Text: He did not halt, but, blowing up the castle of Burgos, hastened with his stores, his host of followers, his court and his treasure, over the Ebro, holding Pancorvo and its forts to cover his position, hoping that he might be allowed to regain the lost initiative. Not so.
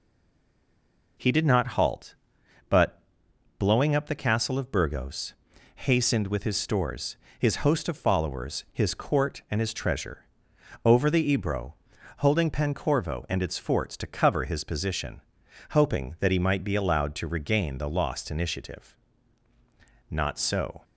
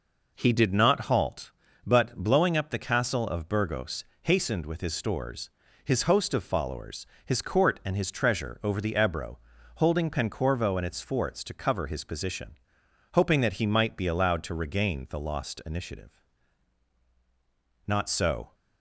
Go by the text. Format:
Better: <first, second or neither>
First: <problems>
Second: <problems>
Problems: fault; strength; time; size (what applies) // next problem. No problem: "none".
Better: second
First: stays silent before the first word; noticeable; until 1.1 s; 1.1 s long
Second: none